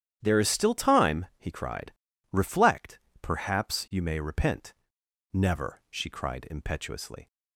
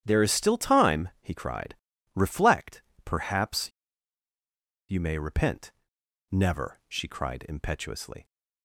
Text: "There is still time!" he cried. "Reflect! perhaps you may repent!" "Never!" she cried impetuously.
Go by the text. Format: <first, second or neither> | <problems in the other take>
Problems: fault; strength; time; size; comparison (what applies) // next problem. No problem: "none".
first | starts louder than the rest; strong; until 1.0 s; 10 dB; strong in the first // pauses between "perhaps" and "you"; at 3.7 s; 1.1 s long